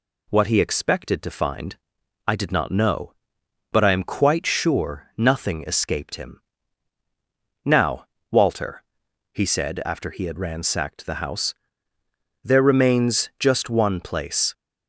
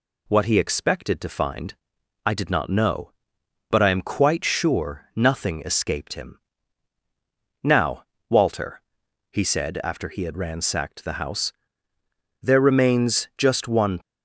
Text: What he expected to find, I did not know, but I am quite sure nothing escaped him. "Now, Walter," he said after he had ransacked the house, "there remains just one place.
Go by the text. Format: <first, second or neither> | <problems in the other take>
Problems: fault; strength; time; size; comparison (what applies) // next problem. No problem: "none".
first | stops before "place"; at 14.0 s